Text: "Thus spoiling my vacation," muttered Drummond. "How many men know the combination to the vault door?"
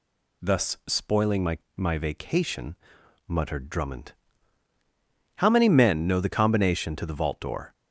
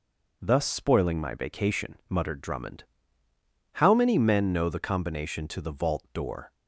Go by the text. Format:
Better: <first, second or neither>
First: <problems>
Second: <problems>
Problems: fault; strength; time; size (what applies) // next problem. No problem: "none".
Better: second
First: says "my" twice; at 1.7 s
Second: none